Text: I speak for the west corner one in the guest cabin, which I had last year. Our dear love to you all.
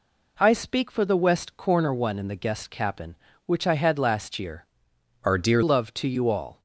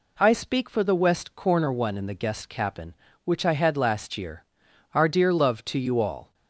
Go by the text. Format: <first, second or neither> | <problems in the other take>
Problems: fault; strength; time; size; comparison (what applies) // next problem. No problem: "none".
second | changes voice from "Our" to "dear"; from 5.2 to 5.6 s; 0.4 s long